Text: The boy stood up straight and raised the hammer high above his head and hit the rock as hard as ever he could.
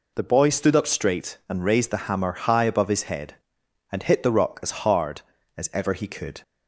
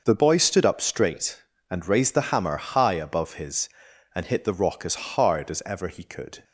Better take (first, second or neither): first